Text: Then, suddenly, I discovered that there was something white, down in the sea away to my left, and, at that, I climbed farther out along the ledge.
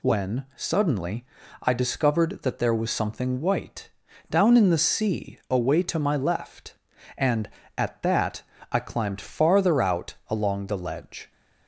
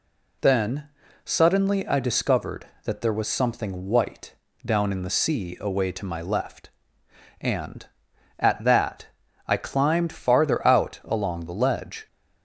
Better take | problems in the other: second | says "When" for "Then"; at 0.0 s

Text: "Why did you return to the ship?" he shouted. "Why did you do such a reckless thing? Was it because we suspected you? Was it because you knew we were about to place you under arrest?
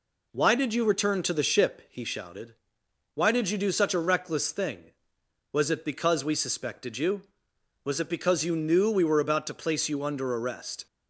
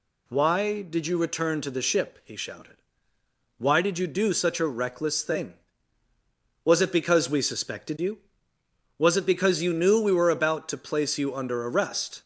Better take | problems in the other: neither | none

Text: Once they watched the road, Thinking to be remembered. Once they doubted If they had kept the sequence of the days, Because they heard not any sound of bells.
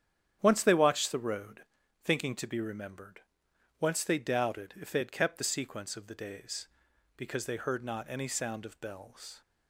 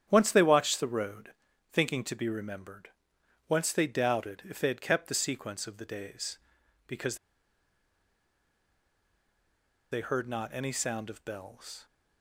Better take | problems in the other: first | starts louder than the rest; strong; until 1.1 s; 10 dB; strong in the first // pauses between "Because" and "they"; strong; at 7.1 s; 2.7 s long

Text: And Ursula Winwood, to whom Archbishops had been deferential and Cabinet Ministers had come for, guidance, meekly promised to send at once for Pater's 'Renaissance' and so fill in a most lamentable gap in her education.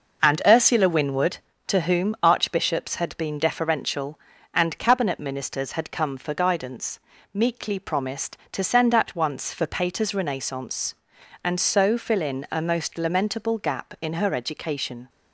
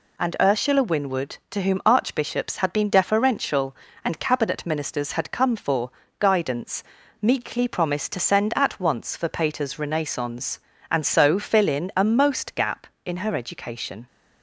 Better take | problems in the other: first | skips "lamentable"; at 12.5 s

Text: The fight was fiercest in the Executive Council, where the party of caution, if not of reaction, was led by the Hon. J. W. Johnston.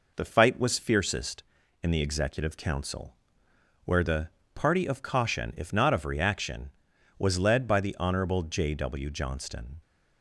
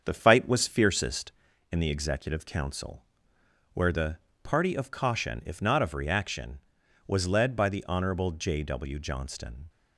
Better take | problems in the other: first | starts louder than the rest; strong; until 1.7 s; 7 dB // pauses between "the" and "party"; slight; at 4.1 s; 0.24 s long; slight in the first

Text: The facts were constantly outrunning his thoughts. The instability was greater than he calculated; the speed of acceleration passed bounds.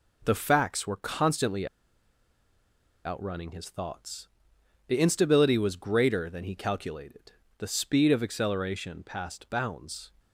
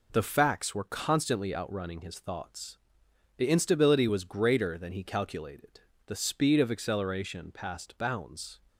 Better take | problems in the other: second | pauses between "constantly" and "outrunning"; strong; at 1.6 s; 1.3 s long

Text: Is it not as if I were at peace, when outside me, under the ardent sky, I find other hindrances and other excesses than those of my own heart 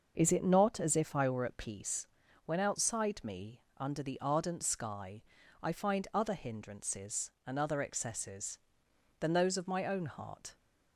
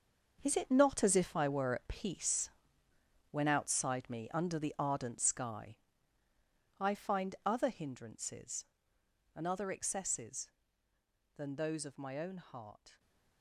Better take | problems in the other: first | gets quieter; strong; throughout; 11.5 dB // stays silent after the last word; slight; from 12.9 s on; 0.5 s long

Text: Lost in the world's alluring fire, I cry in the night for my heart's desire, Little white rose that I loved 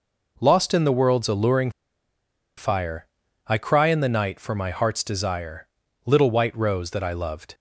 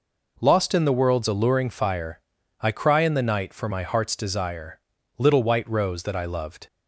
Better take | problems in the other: second | pauses between "alluring" and "fire"; noticeable; at 1.7 s; 0.86 s long

